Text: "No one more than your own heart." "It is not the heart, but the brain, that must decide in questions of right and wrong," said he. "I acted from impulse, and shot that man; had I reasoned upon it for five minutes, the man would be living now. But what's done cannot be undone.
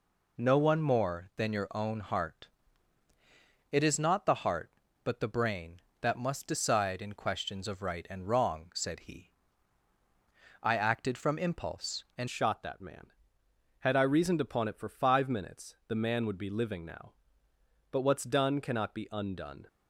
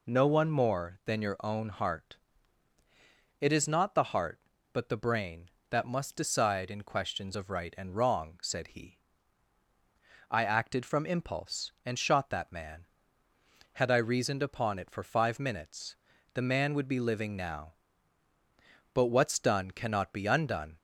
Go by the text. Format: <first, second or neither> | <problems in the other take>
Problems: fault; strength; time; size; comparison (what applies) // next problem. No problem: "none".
second | changes voice at "shot"; from 12.2 s on; 7.4 s long